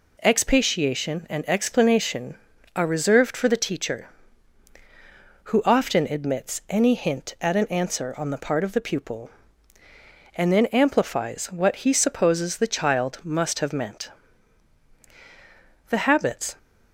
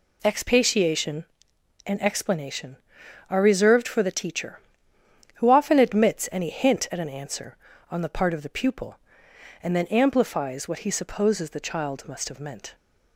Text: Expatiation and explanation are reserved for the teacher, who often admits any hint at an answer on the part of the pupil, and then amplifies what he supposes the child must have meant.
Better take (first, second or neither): second